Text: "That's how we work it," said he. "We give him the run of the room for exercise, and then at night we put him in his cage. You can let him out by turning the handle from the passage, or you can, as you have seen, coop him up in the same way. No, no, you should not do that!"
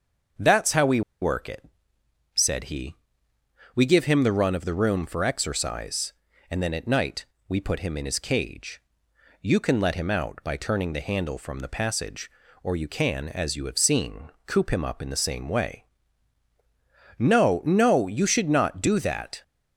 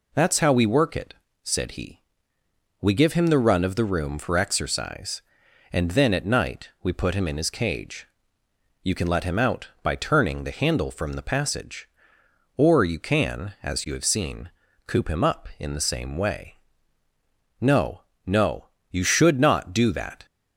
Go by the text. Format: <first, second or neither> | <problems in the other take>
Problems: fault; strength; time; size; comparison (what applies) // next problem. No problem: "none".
second | starts louder than the rest; until 1.6 s; 6.5 dB // pauses between "we" and "work"; slight; at 1.0 s; 0.21 s long // pauses between "night" and "we"; slight; at 7.2 s; 0.24 s long